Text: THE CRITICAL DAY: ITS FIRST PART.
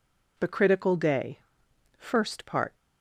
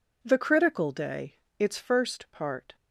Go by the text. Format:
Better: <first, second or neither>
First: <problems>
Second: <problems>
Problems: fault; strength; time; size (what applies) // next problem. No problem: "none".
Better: second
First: skips "ITS"; at 1.6 s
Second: none